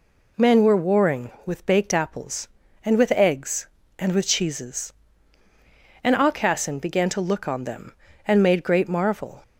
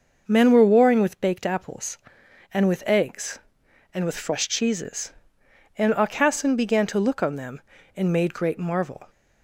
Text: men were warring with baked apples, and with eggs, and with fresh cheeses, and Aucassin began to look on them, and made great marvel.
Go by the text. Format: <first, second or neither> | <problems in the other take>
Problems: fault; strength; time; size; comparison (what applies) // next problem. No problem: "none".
second | skips "fresh"; at 4.2 s